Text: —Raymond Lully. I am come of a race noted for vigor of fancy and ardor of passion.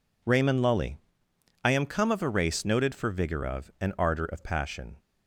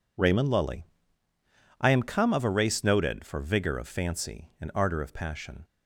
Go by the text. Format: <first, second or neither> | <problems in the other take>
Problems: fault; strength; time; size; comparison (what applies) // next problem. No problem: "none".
second | skips "fancy"; at 3.7 s